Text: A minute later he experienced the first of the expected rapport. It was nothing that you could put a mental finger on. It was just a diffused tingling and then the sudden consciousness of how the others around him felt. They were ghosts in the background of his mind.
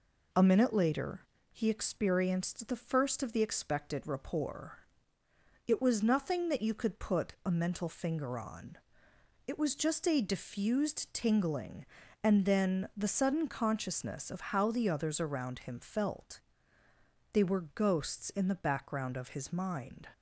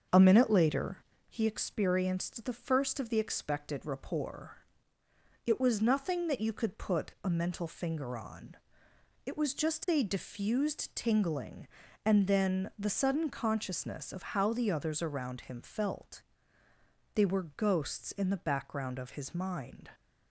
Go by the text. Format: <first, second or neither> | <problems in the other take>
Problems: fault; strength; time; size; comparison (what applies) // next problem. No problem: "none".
first | starts louder than the rest; until 1.4 s; 6.5 dB // pauses between "later" and "he"; slight; at 0.9 s; 0.30 s long; slight in the first